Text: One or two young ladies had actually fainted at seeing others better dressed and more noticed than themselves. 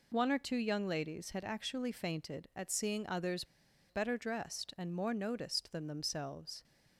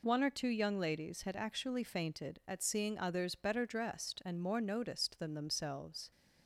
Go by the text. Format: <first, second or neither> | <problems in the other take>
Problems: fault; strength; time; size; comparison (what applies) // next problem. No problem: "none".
second | pauses between "others" and "better"; at 3.4 s; 0.44 s long